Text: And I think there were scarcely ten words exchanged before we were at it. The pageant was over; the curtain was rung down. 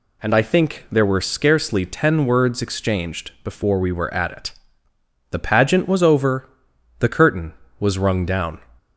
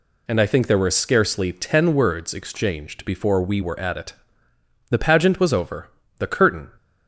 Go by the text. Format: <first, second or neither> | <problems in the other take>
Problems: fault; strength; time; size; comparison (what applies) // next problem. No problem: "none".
first | stops before "was rung down"; at 6.7 s